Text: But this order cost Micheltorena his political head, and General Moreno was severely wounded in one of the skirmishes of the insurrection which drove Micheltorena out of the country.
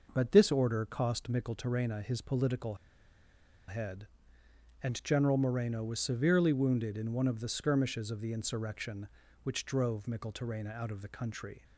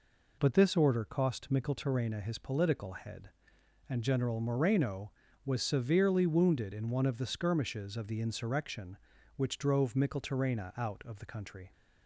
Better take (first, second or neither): second